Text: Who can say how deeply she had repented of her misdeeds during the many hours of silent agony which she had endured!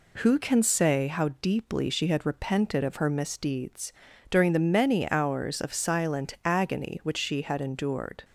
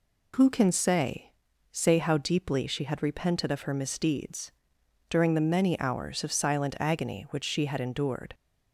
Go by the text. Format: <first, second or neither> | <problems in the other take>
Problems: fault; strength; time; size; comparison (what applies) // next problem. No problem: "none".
first | says "say" twice; at 1.7 s // pauses between "misdeeds" and "during"; noticeable; at 4.5 s; 0.58 s long; also in the first